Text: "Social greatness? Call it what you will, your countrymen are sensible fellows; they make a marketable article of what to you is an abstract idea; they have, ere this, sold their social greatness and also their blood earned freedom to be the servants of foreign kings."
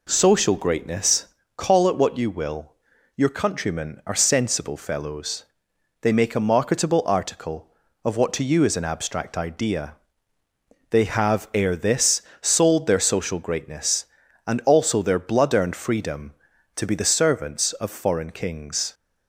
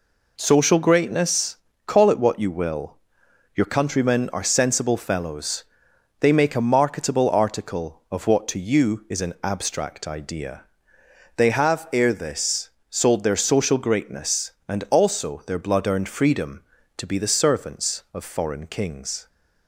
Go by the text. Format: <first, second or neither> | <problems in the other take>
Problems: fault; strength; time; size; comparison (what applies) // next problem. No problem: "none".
neither | none